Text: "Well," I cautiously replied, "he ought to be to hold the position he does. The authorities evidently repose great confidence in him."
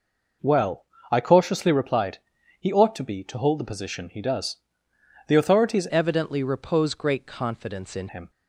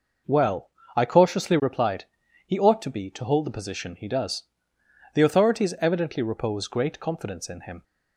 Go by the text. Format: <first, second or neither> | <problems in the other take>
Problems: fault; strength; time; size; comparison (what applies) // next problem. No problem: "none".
second | changes voice from "evidently" to "in"; from 5.8 to 8.0 s; 2.2 s long